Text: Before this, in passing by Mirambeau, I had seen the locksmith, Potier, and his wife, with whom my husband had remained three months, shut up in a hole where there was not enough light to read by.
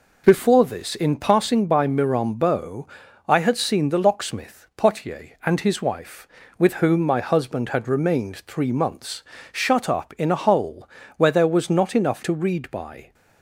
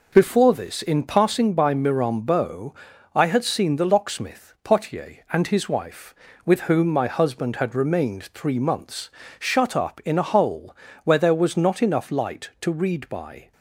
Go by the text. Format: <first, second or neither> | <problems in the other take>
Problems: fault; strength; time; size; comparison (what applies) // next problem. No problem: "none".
second | pauses between "hole" and "where"; slight; at 10.8 s; 0.30 s long; slight in the second // skips "light"; at 12.2 s